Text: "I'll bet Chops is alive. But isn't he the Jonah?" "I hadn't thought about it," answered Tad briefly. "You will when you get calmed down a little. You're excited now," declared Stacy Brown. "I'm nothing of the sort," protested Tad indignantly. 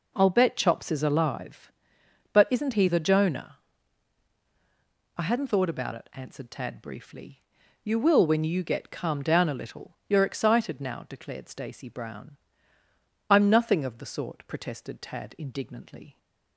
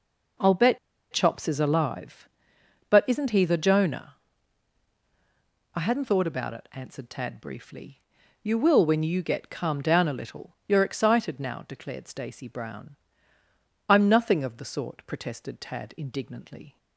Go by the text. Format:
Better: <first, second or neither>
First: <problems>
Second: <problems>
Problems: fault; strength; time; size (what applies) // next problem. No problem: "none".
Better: first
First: none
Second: pauses between "bet" and "Chops"; slight; at 0.7 s; 0.34 s long